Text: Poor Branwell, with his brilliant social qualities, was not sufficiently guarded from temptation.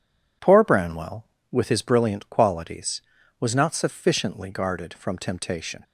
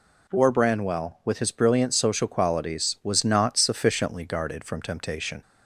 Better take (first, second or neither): second